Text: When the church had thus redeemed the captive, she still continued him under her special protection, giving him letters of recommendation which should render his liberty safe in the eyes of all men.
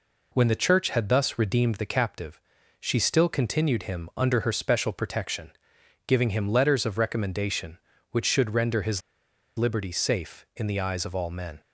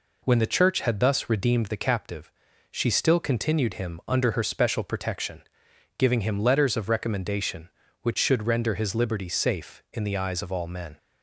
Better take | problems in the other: second | pauses between "his" and "liberty"; noticeable; at 9.0 s; 0.57 s long

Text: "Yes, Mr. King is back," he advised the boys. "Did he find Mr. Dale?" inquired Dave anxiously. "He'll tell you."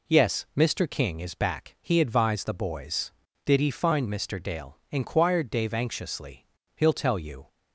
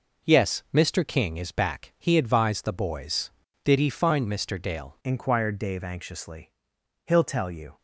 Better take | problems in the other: first | changes voice at "inquired"; from 5.0 s on; 2.7 s long

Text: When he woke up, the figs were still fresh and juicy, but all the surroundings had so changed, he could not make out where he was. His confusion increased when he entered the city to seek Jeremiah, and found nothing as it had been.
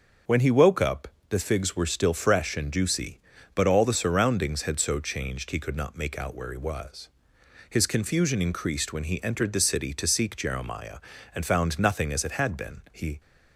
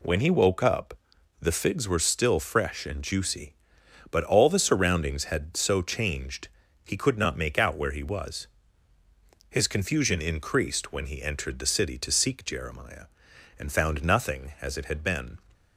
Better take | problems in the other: second | starts louder than the rest; until 1.4 s; 6.5 dB // goes on to say "He"; slight; from 12.9 s on; 0.28 s long

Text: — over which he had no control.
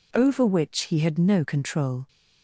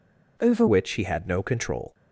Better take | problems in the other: first | changes voice at "which"; from 0.6 s on; 1.3 s long

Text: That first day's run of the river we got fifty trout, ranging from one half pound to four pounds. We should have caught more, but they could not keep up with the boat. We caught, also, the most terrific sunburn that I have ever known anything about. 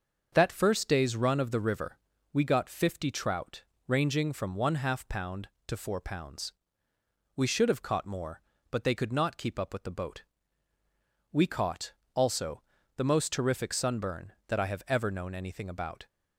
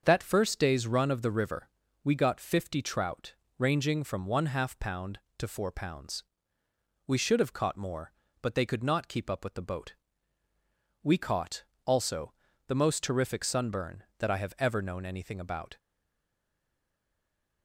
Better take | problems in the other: first | starts louder than the rest; until 1.0 s; 6.5 dB; also in the first // pauses between "river" and "we"; slight; at 1.6 s; 0.34 s long; slight in the first // stays silent after the last word; noticeable; from 15.7 s on; 1.9 s long

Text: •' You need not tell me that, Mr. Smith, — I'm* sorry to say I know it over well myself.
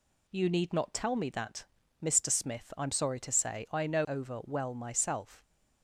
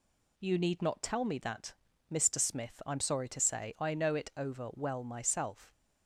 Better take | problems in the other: second | skips "it"; at 4.0 s

